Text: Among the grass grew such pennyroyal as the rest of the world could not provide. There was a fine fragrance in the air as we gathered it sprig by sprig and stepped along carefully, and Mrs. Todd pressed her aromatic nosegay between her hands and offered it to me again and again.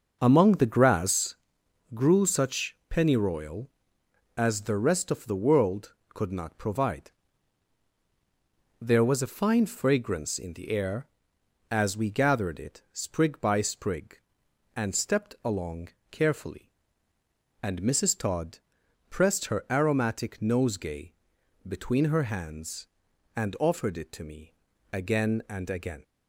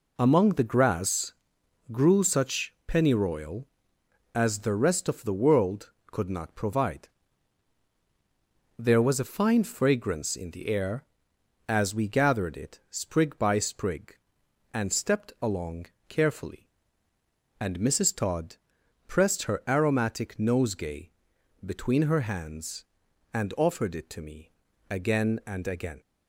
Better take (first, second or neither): second